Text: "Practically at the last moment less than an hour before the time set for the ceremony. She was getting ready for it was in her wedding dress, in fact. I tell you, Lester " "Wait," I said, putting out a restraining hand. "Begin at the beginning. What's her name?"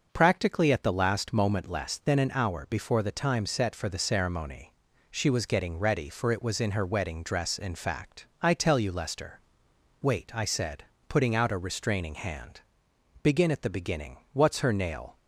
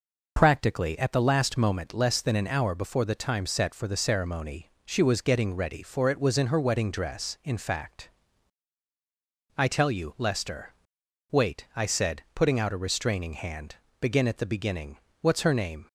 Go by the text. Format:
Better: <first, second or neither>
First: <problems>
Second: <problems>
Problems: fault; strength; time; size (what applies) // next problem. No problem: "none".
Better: second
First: says "nail" for "name"; at 14.7 s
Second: none